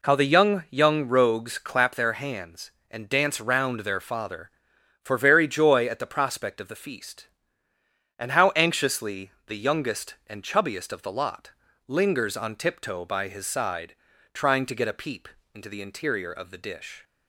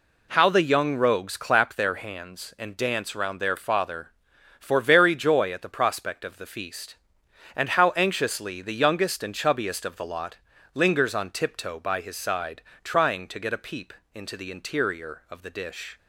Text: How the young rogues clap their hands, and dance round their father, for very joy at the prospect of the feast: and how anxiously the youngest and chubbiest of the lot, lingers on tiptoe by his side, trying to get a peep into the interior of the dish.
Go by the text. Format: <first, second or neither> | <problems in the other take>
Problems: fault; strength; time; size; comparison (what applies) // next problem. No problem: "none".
second | says "young" twice; at 0.6 s // pauses between "anxiously" and "the"; slight; at 9.3 s; 0.16 s long // pauses between "peep" and "into"; slight; at 15.2 s; 0.26 s long; slight in the second